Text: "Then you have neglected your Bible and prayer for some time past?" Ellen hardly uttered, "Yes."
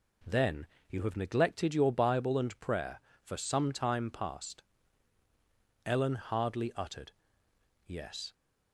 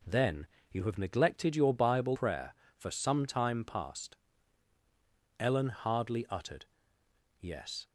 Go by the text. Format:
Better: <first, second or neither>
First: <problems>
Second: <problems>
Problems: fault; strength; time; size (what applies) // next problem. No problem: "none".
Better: first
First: pauses between "Then" and "you"; slight; at 0.6 s; 0.24 s long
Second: pauses between "Then" and "you"; slight; at 0.4 s; 0.26 s long // skips "and"; at 2.1 s